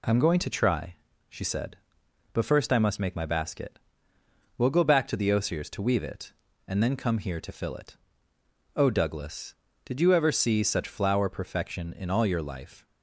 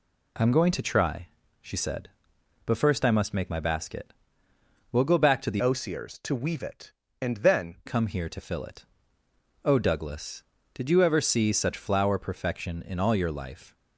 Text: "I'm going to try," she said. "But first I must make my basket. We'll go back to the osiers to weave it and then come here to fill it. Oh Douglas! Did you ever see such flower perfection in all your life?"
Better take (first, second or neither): first